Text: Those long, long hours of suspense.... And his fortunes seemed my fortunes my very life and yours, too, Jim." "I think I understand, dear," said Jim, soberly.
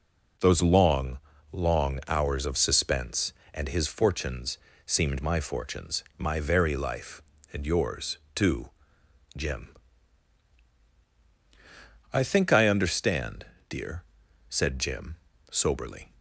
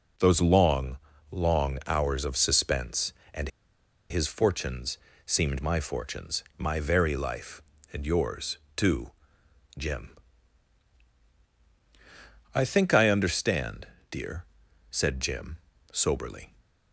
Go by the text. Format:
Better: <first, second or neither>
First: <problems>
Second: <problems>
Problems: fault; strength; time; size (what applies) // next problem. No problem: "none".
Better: first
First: pauses between "fortunes" and "seemed"; slight; at 4.5 s; 0.26 s long // pauses between "fortunes" and "my"; slight; at 6.0 s; 0.16 s long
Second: pauses between "And" and "his"; noticeable; at 3.4 s; 0.61 s long // pauses between "fortunes" and "seemed"; slight; at 4.9 s; 0.26 s long // pauses between "fortunes" and "my"; slight; at 6.4 s; 0.16 s long